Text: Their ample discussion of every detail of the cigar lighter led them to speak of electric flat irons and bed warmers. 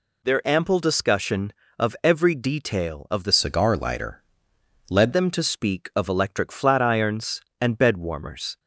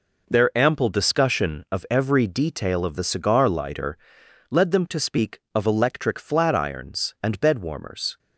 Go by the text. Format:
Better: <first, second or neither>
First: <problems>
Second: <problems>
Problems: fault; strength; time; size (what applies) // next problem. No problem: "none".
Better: second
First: changes voice from "cigar" to "led"; from 3.3 to 5.1 s; 1.8 s long // pauses between "lighter" and "led"; noticeable; at 4.2 s; 0.66 s long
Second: pauses between "lighter" and "led"; noticeable; at 3.9 s; 0.54 s long